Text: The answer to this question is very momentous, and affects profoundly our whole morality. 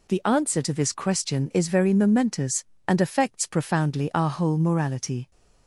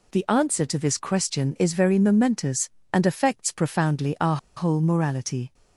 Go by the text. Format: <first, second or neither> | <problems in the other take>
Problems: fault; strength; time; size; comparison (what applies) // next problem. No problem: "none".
first | pauses between "our" and "whole"; slight; at 4.3 s; 0.19 s long